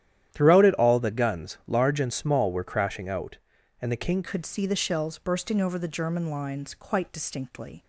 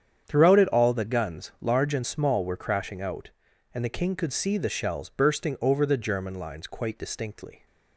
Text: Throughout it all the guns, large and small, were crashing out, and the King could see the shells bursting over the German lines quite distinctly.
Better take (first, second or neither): second